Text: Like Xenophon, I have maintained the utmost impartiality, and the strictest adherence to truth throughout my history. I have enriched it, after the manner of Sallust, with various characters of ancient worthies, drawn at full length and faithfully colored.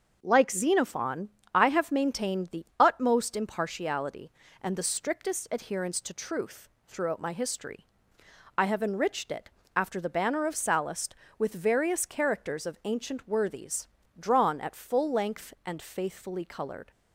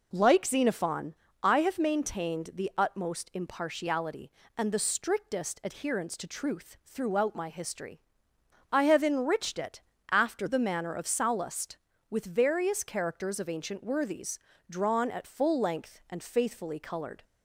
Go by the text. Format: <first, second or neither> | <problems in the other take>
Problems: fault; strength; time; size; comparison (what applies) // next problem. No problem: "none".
second | starts louder than the rest; until 1.2 s; 6.5 dB // pauses between "the" and "utmost"; slight; at 2.6 s; 0.16 s long // pauses between "truth" and "throughout"; slight; at 6.6 s; 0.20 s long // says "banner" for "manner"; at 10.0 s